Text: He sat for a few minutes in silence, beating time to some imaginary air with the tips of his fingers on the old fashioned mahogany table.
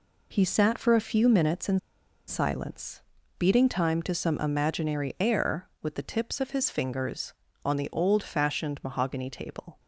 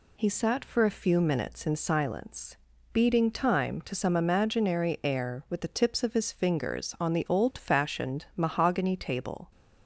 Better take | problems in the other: second | pauses between "in" and "silence"; noticeable; at 1.7 s; 0.50 s long

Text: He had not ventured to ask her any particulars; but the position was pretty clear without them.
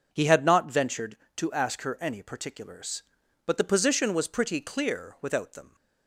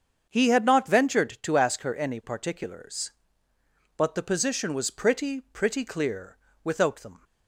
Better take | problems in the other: first | starts louder than the rest; strong; until 1.3 s; 7 dB // says "pretty" twice; at 5.3 s // pauses between "clear" and "without"; slight; at 6.3 s; 0.24 s long

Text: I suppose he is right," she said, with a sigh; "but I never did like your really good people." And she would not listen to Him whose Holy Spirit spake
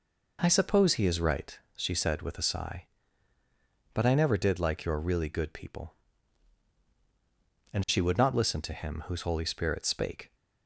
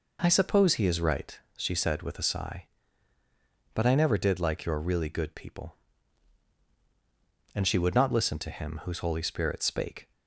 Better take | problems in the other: neither | none

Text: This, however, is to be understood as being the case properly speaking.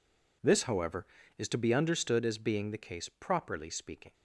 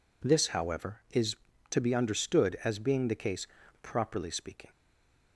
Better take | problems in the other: first | pauses between "case" and "properly"; slight; at 3.4 s; 0.36 s long // stays silent after the last word; slight; from 4.7 s on; 0.6 s long

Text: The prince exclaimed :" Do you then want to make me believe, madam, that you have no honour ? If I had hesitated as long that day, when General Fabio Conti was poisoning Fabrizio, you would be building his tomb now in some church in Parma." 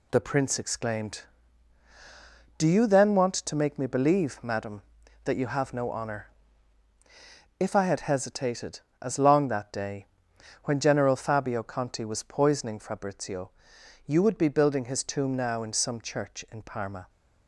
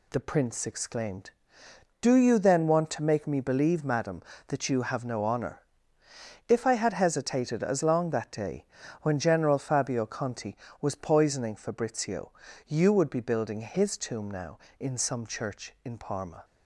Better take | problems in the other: neither | none

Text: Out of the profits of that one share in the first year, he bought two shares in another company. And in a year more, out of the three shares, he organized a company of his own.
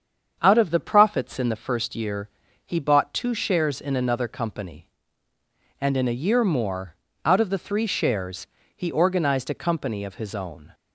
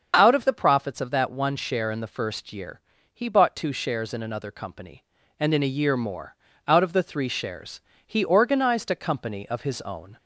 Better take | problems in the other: second | starts louder than the rest; strong; until 1.4 s; 7.5 dB; also in the second // skips "of that one share"; at 1.3 s

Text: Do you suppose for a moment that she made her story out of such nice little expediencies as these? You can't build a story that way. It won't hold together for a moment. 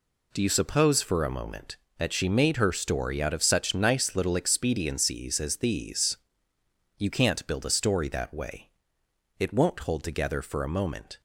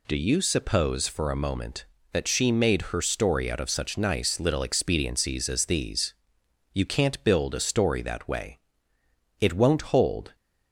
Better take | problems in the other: first | stops before "together for a moment"; at 10.3 s

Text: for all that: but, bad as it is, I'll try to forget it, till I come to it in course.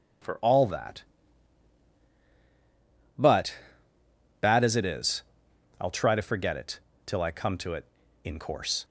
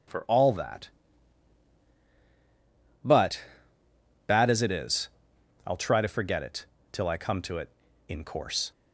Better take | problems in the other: neither | none

